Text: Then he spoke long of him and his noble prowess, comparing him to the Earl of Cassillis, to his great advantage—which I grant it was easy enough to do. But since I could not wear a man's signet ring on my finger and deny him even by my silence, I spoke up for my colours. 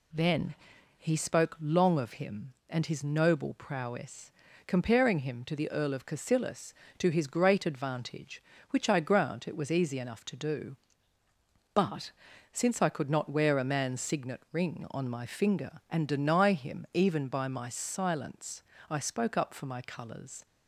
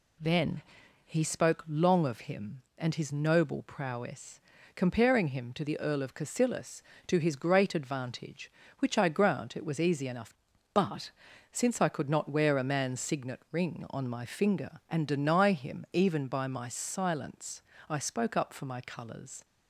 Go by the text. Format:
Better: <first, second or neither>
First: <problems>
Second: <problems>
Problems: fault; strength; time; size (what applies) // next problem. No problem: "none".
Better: first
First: pauses between "Then" and "he"; at 0.5 s; 0.42 s long // pauses between "But" and "since"; at 12.1 s; 0.40 s long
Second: pauses between "Then" and "he"; at 0.6 s; 0.42 s long // skips "to do"; at 10.5 s // pauses between "But" and "since"; at 11.1 s; 0.40 s long